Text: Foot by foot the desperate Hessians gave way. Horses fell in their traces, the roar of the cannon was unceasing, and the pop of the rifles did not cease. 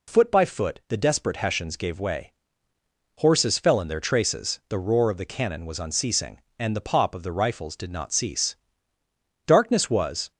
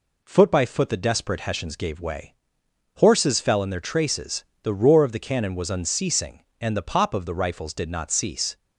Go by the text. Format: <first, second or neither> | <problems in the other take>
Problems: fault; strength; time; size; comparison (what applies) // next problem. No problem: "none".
second | goes on to say "Darkness was"; noticeable; from 9.4 s on; 0.86 s long